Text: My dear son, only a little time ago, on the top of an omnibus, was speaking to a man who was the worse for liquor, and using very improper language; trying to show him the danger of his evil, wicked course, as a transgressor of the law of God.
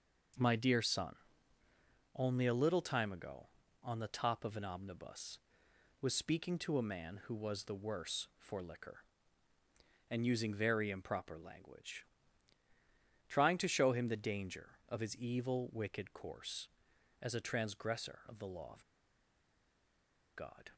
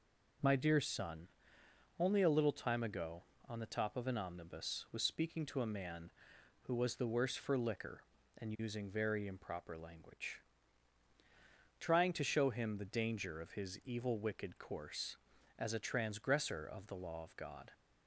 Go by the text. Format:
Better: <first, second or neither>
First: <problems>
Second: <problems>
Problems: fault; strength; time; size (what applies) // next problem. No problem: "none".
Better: second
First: pauses between "of" and "God"; strong; at 18.8 s; 1.5 s long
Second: none